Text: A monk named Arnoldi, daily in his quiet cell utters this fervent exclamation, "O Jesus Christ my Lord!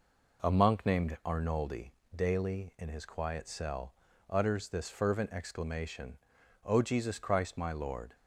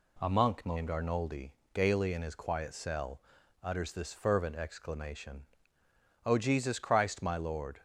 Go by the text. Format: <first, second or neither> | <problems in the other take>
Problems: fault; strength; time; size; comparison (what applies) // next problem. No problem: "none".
first | says "gaily" for "daily"; at 1.7 s // pauses between "cell" and "utters"; at 3.2 s; 0.40 s long; slight in the first